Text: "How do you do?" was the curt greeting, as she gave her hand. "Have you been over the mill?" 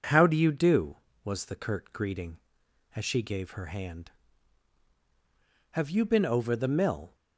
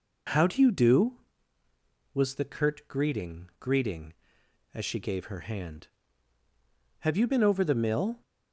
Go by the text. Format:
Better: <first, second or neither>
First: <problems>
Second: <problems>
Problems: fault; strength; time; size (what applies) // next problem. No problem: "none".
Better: first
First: none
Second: says "greeting" twice; at 3.5 s